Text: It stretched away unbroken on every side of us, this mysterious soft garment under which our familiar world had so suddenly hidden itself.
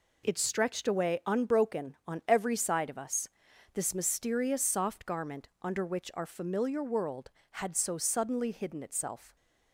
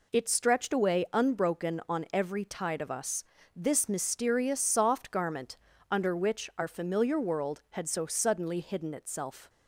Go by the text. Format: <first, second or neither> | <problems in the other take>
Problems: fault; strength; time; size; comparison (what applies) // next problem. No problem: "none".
first | says "tide" for "side"; at 2.4 s // pauses between "garment" and "under"; slight; at 5.5 s; 0.34 s long